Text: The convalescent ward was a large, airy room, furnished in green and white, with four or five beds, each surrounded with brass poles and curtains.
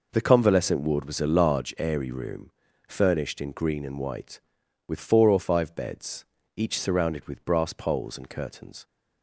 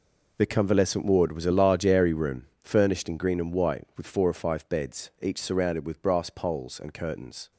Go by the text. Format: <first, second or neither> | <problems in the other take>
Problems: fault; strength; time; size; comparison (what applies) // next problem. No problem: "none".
neither | none